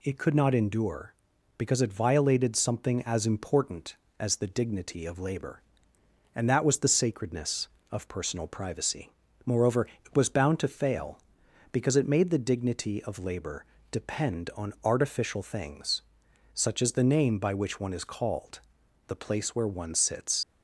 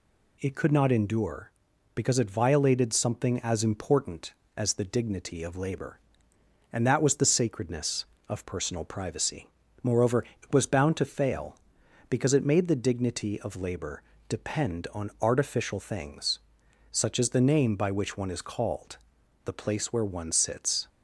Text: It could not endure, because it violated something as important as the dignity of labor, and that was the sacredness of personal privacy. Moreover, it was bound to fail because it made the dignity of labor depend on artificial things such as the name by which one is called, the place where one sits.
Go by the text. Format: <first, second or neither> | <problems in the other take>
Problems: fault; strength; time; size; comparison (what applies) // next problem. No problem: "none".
second | pauses between "labor" and "depend"; slight; at 13.6 s; 0.26 s long; slight in the second // pauses between "things" and "such"; noticeable; at 16.0 s; 0.54 s long; noticeable in the second // leaves "sits" unfinished; at 20.4 s; 75 ms